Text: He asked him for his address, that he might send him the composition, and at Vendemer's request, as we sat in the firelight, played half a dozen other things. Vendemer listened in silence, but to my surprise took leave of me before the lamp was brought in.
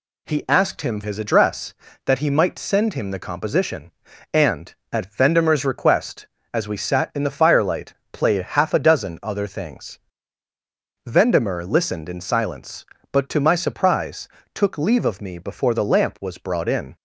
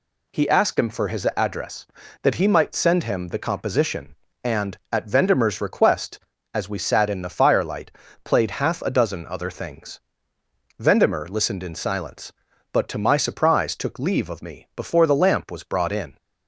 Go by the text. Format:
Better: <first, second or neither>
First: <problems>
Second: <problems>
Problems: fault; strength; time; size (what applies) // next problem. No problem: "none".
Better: second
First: skips "for"; at 1.0 s // pauses between "surprise" and "took"; slight; at 14.2 s; 0.26 s long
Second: none